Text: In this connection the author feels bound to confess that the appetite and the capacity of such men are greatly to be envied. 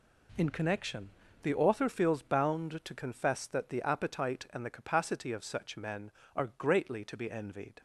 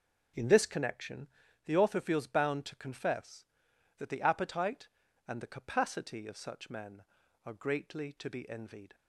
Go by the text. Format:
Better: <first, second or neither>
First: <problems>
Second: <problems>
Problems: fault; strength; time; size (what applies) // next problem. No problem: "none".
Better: second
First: skips "this"; at 0.5 s // pauses between "connection" and "the"; slight; at 1.1 s; 0.32 s long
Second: pauses between "connection" and "the"; slight; at 1.2 s; 0.36 s long